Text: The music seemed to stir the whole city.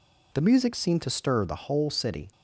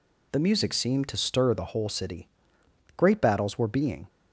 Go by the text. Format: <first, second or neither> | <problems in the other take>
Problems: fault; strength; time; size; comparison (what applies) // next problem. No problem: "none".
first | goes on to say "Great battles were being"; noticeable; from 2.9 s on; 1.1 s long